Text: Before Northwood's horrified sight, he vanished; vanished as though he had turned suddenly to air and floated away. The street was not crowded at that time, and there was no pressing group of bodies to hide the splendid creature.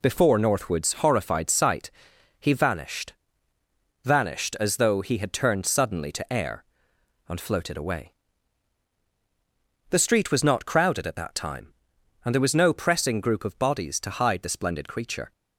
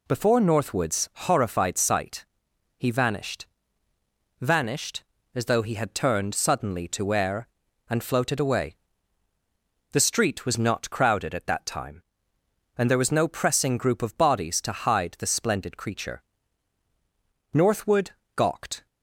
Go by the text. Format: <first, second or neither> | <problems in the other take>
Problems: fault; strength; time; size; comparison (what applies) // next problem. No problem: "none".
first | goes on to say "Northwood gawked"; from 17.5 s on; 1.3 s long